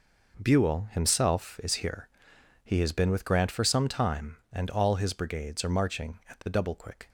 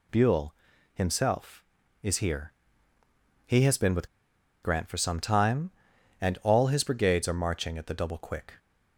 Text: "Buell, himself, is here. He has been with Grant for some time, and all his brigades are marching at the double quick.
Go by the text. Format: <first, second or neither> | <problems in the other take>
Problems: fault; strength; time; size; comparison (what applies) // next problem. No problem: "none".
first | pauses between "with" and "Grant"; noticeable; at 4.0 s; 0.55 s long